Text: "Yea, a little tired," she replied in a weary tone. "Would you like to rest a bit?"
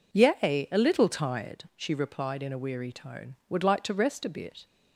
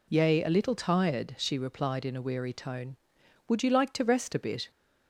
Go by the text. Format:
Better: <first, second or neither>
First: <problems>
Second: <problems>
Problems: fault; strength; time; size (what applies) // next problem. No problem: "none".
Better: second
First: skips "you"; at 3.6 s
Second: none